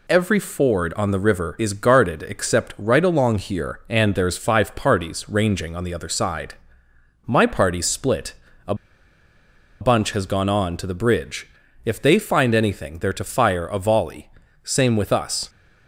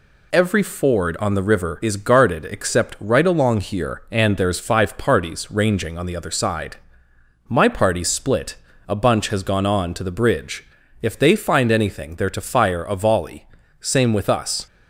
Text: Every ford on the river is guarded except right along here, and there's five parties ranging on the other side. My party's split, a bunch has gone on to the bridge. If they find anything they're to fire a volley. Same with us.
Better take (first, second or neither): second